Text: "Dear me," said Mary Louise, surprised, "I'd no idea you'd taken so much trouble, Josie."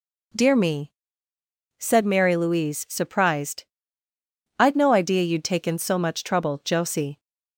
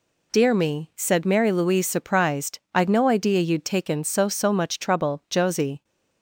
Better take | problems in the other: first | says "so" twice; at 4.2 s

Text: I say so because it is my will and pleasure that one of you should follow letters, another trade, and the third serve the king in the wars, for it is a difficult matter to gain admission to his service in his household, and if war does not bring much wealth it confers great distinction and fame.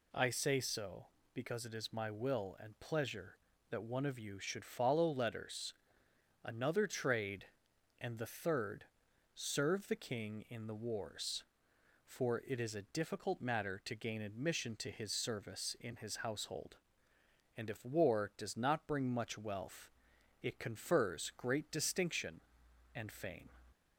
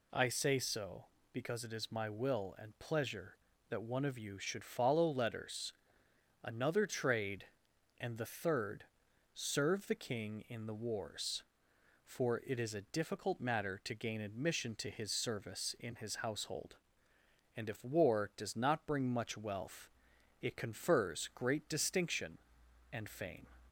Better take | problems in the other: neither | pauses between "third" and "serve"; noticeable; the same in both // pauses between "wealth" and "it"; noticeable; the same in both

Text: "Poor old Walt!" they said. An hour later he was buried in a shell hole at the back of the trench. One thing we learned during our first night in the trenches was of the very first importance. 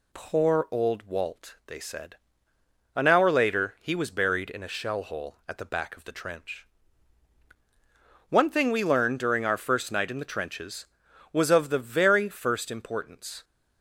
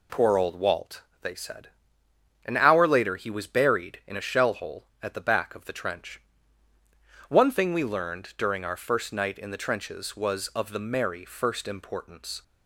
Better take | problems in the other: first | says "merry" for "very"; at 10.8 s

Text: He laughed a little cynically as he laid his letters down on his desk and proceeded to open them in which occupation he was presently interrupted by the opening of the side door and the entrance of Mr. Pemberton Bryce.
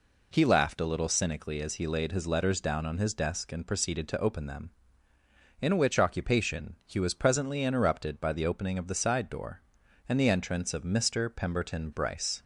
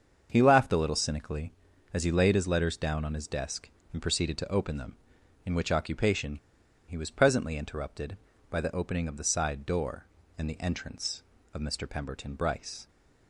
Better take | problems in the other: first | starts louder than the rest; until 1.3 s; 7 dB // pauses between "occupation" and "he"; noticeable; at 6.3 s; 0.51 s long

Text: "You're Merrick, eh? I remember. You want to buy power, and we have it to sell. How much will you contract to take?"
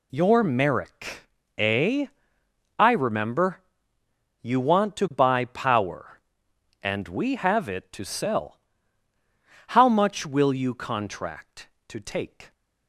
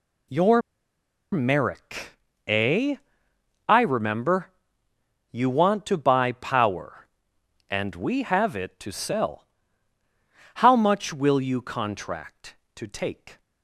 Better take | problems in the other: first | pauses between "You're" and "Merrick"; noticeable; at 0.6 s; 0.72 s long

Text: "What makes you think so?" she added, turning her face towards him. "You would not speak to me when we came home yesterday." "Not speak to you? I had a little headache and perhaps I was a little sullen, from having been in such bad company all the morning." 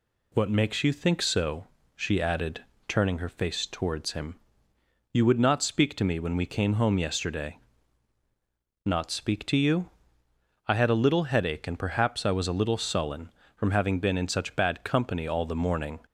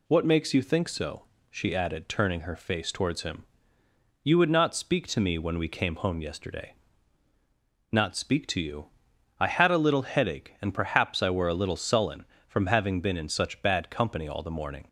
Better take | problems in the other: first | says "were" for "was"; at 11.2 s

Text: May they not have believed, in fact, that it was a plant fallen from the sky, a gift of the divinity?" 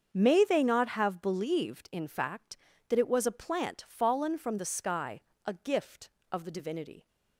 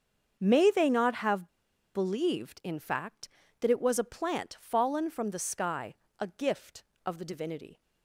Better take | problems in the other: first | starts louder than the rest; until 1.4 s; 7 dB; also in the first // pauses between "have" and "believed"; noticeable; at 1.4 s; 0.47 s long

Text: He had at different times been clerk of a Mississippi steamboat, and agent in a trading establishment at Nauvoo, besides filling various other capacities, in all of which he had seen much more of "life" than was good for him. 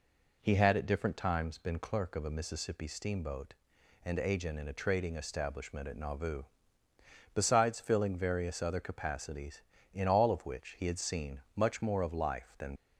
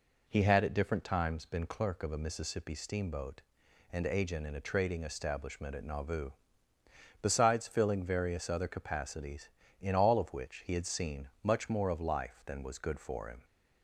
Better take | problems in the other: second | stops before "was good for him"; at 12.7 s

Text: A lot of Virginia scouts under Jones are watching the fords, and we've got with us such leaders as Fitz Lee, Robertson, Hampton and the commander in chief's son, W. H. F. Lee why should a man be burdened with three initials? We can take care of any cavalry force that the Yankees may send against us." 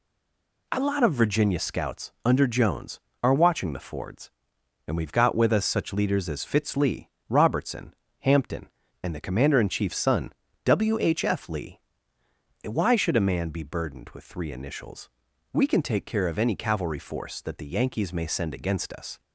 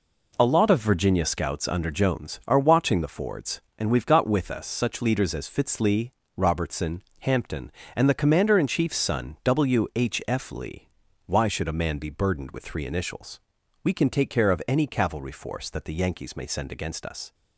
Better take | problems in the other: second | stays silent before the first word; slight; until 0.6 s; 0.6 s long // pauses between "Lee" and "why"; noticeable; at 11.7 s; 0.86 s long; also in the second

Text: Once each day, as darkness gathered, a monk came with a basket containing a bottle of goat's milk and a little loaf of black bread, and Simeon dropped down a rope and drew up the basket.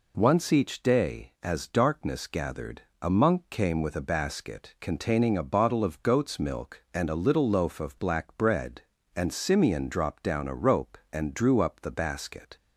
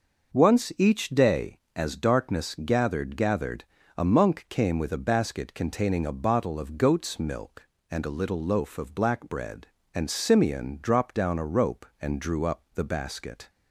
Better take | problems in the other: first | says "gathered" twice; at 3.1 s

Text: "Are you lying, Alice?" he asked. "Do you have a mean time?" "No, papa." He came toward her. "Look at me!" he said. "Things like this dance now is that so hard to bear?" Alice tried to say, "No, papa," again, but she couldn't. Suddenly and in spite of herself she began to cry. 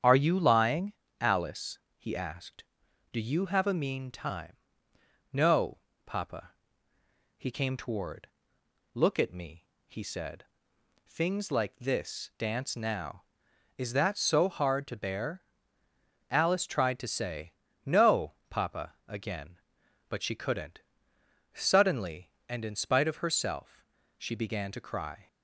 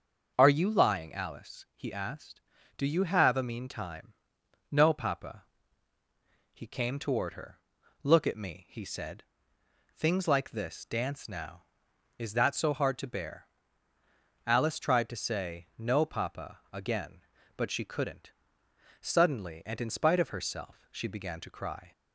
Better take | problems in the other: second | starts louder than the rest; strong; until 1.2 s; 8.5 dB; also in the second // skips "her"; at 8.6 s // pauses between "herself" and "she"; slight; at 23.8 s; 0.34 s long

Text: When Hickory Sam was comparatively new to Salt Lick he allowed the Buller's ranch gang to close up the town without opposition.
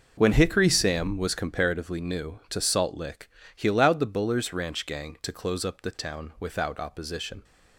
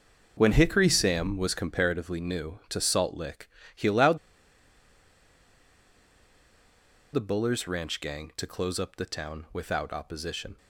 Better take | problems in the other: first | pauses between "Lick" and "he"; slight; at 3.4 s; 0.26 s long; slight in the first // pauses between "allowed" and "the"; strong; at 4.1 s; 2.9 s long

